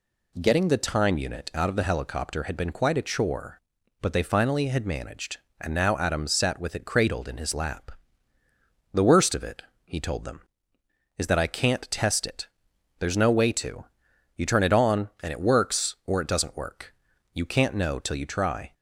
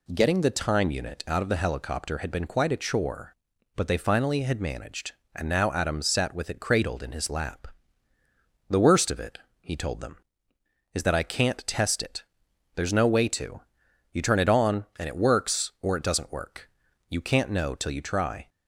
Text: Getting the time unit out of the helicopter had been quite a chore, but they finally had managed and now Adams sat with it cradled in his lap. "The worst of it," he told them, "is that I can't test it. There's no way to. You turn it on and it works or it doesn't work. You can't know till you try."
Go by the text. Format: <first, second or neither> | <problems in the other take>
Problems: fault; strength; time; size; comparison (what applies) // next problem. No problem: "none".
neither | none